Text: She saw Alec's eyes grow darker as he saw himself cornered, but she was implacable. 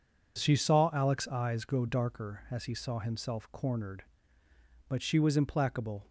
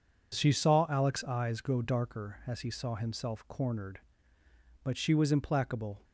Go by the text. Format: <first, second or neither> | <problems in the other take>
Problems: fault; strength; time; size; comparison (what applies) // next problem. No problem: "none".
neither | none